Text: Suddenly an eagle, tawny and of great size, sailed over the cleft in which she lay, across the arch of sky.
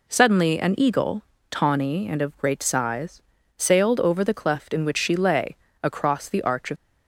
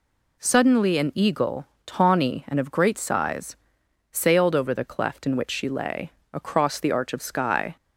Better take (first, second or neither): second